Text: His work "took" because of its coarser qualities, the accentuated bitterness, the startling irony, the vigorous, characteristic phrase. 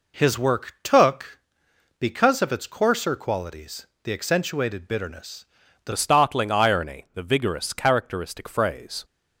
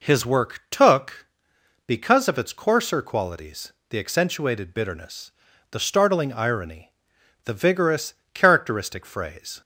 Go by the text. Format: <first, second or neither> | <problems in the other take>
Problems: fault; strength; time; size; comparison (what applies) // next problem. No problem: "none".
second | changes voice at "startling"; from 5.9 s on; 3.1 s long